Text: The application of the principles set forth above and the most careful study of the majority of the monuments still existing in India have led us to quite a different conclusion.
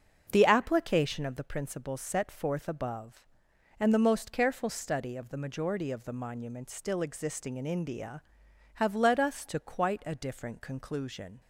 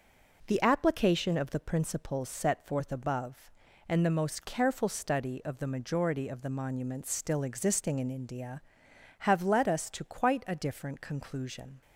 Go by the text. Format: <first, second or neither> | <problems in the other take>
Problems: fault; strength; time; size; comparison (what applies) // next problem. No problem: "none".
second | starts louder than the rest; until 1.3 s; 6.5 dB